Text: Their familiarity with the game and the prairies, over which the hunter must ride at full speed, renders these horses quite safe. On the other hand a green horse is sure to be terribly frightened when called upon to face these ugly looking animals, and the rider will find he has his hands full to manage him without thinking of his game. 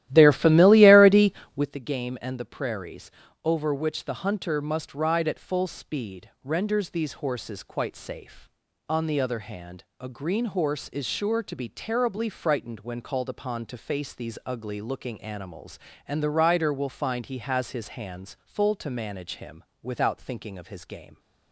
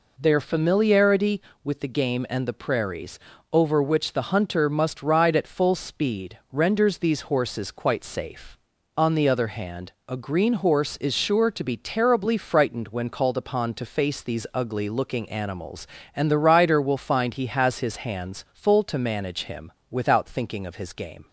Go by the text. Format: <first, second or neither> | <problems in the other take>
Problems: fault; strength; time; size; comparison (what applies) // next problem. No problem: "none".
second | starts louder than the rest; strong; until 1.7 s; 14 dB // pauses between "hand" and "a"; slight; at 9.8 s; 0.16 s long; slight in the second // pauses between "him" and "without"; slight; at 19.6 s; 0.20 s long; slight in the second